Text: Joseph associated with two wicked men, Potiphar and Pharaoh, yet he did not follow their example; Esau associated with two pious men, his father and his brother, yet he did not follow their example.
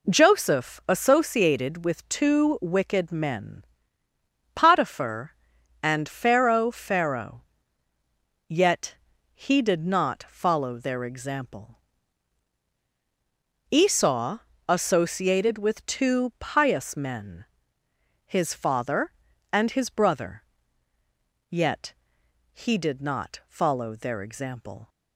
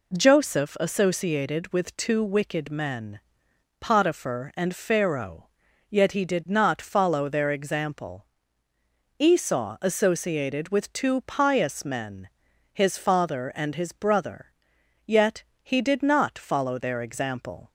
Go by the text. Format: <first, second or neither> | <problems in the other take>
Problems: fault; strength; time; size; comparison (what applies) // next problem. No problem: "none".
second | says "Pharaoh" twice; at 6.7 s // pauses between "yet" and "he"; slight; at 8.9 s; 0.36 s long // pauses between "Esau" and "associated"; slight; at 14.4 s; 0.28 s long // pauses between "yet" and "he"; noticeable; at 21.9 s; 0.60 s long; slight in the second